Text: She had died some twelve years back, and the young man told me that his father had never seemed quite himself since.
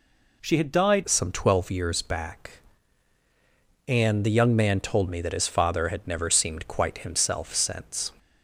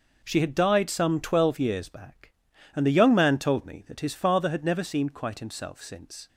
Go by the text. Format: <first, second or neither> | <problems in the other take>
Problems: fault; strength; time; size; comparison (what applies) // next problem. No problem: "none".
second | changes voice at "some"; from 1.0 s on; 7.1 s long